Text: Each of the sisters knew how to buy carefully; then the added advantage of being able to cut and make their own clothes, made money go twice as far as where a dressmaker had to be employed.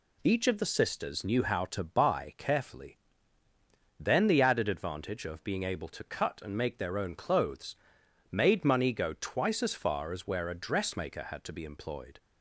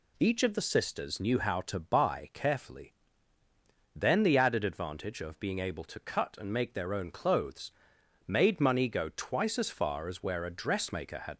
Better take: first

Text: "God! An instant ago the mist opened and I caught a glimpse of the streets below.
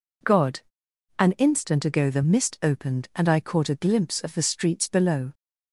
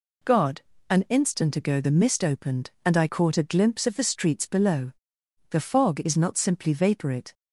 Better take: first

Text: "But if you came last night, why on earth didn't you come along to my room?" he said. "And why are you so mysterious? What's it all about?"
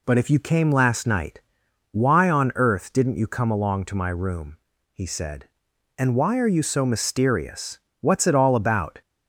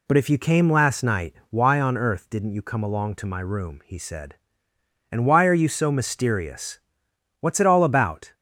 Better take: neither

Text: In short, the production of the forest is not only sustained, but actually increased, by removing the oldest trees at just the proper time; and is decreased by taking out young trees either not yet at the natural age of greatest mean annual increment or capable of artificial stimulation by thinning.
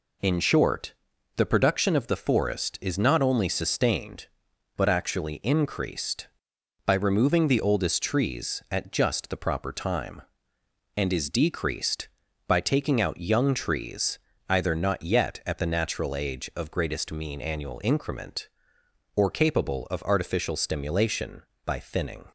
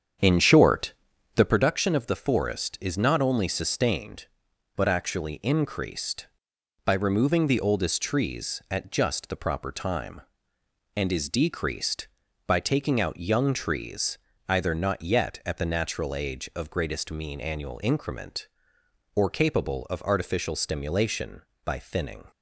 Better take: first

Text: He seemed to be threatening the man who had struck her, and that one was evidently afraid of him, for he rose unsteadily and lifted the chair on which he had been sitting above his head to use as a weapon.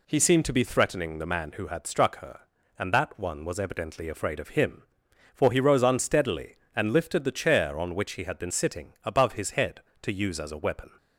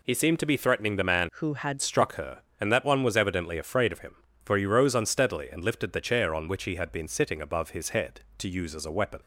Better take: first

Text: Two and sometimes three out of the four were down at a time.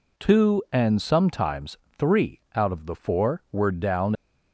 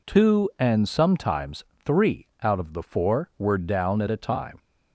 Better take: second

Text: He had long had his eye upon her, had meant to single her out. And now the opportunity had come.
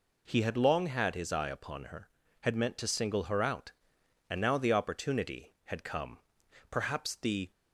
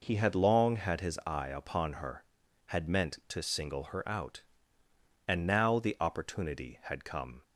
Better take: second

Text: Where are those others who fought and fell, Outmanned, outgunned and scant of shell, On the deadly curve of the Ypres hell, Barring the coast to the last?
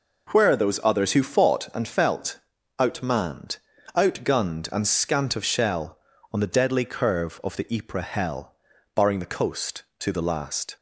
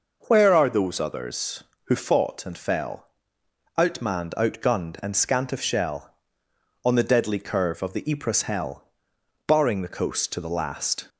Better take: second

